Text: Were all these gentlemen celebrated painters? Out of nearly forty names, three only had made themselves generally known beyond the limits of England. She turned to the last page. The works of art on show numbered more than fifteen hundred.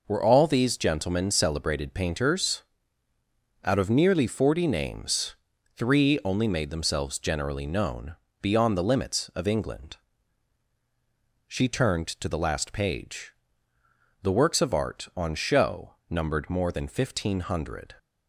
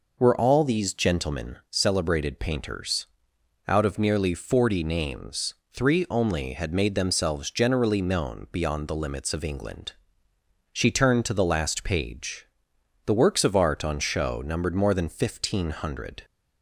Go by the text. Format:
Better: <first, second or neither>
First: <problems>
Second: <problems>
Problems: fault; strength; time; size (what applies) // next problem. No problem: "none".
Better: second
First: skips "had"; at 6.4 s // pauses between "known" and "beyond"; slight; at 8.1 s; 0.28 s long // pauses between "show" and "numbered"; slight; at 15.9 s; 0.16 s long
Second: none